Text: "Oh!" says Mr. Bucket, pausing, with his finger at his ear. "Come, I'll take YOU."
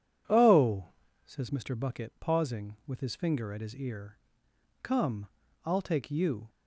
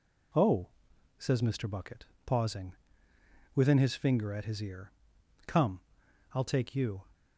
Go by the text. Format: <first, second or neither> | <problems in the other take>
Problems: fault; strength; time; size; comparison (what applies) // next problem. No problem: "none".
first | says "within" for "with"; at 3.5 s